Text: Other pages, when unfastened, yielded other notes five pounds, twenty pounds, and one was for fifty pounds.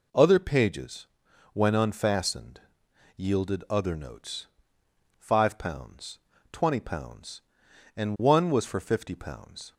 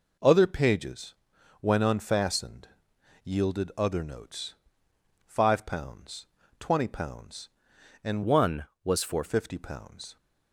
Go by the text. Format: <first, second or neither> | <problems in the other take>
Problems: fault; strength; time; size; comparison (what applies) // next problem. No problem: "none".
first | pauses between "notes" and "five"; noticeable; at 4.5 s; 0.72 s long; noticeable in the first // changes voice from "one" to "for"; from 8.2 to 9.2 s; 1.0 s long